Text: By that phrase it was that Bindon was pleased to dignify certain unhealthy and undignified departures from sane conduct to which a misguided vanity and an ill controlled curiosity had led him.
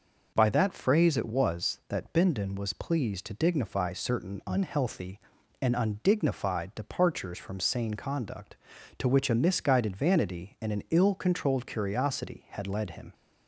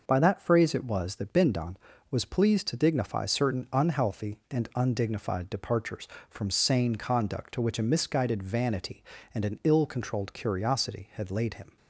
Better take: first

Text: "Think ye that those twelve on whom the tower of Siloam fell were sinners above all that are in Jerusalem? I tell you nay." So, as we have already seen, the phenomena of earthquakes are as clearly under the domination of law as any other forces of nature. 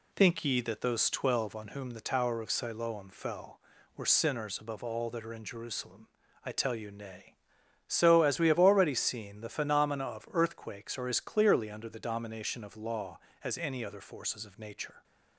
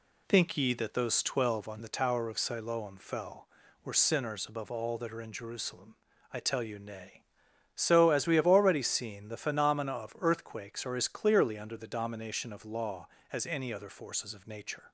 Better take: first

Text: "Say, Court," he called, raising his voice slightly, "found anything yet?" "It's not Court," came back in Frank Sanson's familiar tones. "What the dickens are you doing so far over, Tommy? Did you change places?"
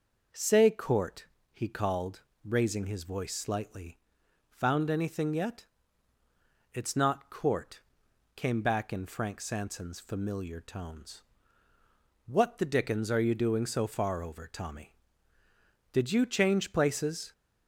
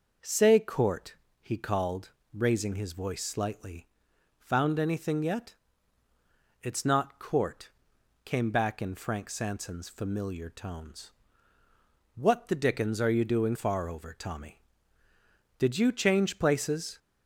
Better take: first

